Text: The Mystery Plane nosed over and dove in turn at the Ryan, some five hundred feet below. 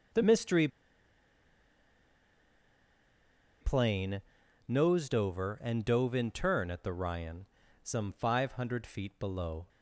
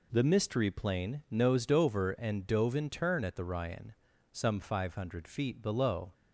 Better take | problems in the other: second | starts louder than the rest; until 4.0 s; 6.5 dB // pauses between "Mystery" and "Plane"; strong; at 0.6 s; 2.9 s long // pauses between "Plane" and "nosed"; at 4.2 s; 0.44 s long

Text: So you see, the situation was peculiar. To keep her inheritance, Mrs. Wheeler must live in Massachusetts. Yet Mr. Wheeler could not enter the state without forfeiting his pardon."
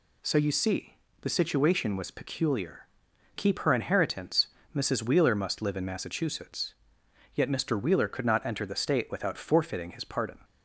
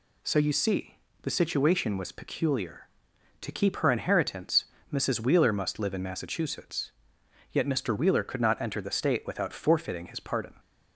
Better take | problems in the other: second | skips "To"; at 3.1 s

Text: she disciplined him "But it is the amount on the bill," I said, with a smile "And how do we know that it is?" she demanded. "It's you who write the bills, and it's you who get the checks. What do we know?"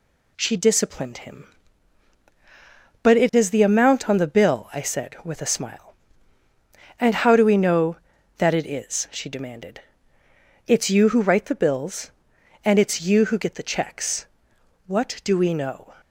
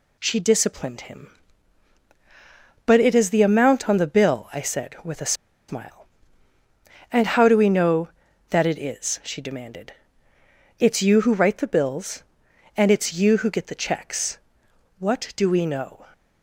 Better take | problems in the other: first | pauses between "a" and "smile"; slight; at 5.3 s; 0.35 s long

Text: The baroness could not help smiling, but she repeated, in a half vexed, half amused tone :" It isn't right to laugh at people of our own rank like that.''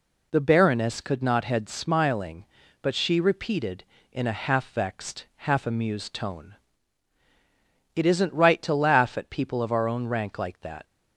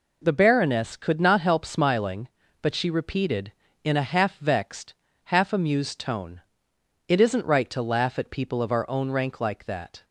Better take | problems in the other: second | says "head" for "help"; at 1.4 s

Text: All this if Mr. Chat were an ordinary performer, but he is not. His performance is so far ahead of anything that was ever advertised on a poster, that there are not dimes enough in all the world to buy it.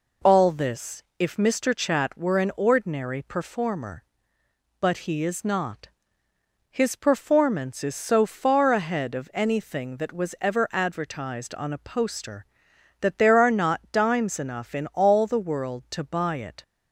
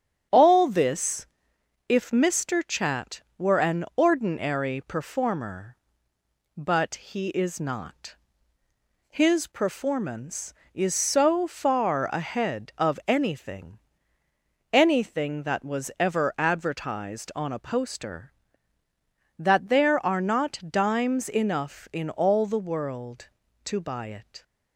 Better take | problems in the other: first | starts louder than the rest; strong; until 1.9 s; 9.5 dB // pauses between "this" and "if"; noticeable; at 1.2 s; 0.62 s long; slight in the first // says "anything" twice; at 14.7 s

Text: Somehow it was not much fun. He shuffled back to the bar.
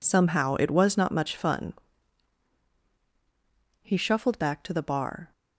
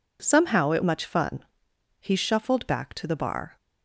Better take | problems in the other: first | skips "was not"; at 0.8 s

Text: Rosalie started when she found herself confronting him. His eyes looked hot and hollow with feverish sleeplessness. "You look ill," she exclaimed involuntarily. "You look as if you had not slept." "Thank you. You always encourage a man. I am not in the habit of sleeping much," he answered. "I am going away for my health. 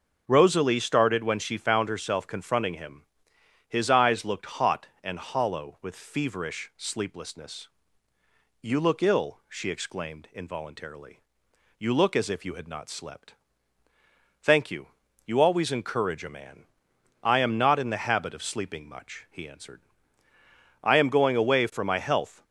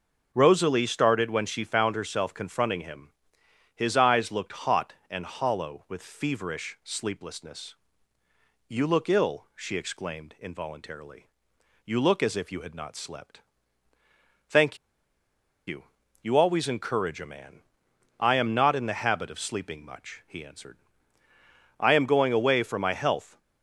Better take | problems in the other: first | starts louder than the rest; noticeable; until 1.3 s; 6 dB // pauses between "Thank" and "you"; noticeable; at 14.7 s; 0.90 s long

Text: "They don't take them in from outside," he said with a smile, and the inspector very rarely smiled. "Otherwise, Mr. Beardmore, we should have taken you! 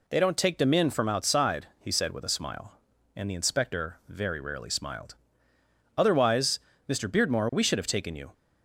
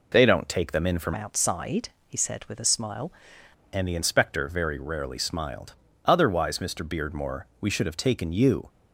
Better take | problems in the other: first | changes voice from "outside" to "smile"; from 1.1 to 3.1 s; 2.0 s long

